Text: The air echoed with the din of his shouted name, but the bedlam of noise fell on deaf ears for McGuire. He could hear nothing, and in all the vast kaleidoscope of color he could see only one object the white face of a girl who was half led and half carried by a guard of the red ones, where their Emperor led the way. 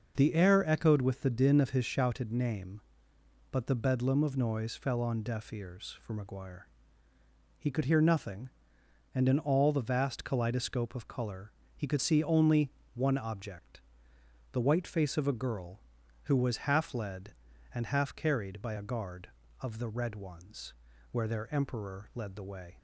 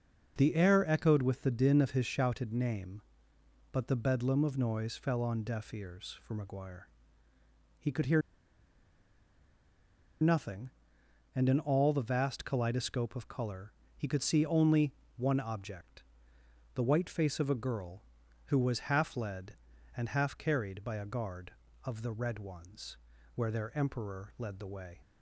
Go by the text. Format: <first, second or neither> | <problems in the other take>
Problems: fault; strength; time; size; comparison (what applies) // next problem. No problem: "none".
first | pauses between "hear" and "nothing"; strong; at 8.2 s; 2.0 s long // pauses between "color" and "he"; slight; at 13.7 s; 0.24 s long; slight in the first // pauses between "only" and "one"; slight; at 14.9 s; 0.24 s long; slight in the first // pauses between "object" and "the"; noticeable; at 16.0 s; 0.72 s long; noticeable in the first